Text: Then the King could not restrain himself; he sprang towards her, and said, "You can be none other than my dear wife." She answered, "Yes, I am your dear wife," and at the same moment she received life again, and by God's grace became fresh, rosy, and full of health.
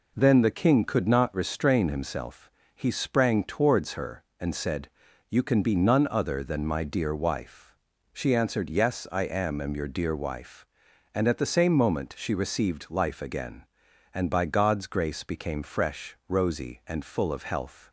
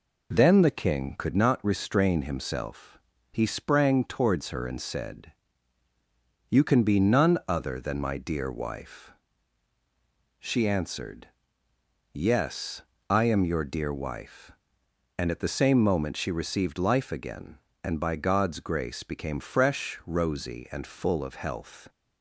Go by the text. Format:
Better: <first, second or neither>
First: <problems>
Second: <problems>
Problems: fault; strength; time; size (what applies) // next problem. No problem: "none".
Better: second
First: says "am" twice; at 9.5 s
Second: none